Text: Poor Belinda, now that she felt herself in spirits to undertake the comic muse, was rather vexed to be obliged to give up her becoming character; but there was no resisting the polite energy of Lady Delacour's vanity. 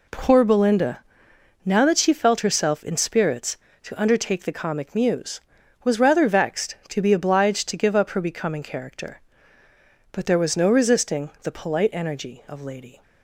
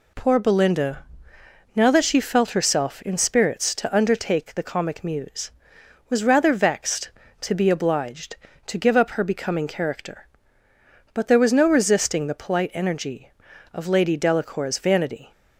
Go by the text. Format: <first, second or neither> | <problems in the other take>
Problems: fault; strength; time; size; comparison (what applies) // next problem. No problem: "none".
second | stops before "Delacour's vanity"; at 13.0 s